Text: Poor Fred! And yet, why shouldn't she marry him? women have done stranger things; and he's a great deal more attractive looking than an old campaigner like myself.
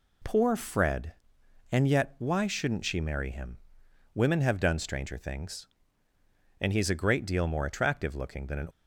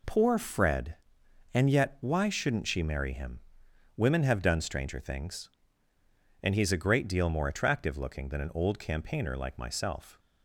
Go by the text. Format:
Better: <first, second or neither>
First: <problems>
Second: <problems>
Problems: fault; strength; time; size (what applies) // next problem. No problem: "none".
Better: second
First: stops before "old campaigner like myself"; at 8.7 s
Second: none